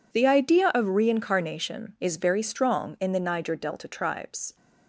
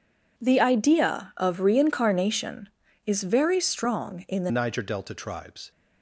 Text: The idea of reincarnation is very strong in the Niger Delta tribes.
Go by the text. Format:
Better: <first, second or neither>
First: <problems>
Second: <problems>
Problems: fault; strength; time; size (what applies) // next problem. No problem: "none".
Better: first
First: none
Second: changes voice at "Niger"; from 4.5 s on; 1.2 s long